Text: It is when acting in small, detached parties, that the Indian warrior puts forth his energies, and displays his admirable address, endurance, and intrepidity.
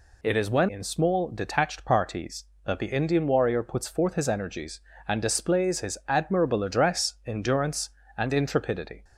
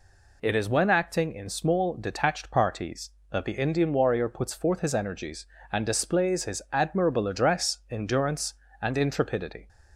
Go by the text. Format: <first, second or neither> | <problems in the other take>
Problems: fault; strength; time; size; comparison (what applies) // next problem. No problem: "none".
second | skips "acting"; at 0.6 s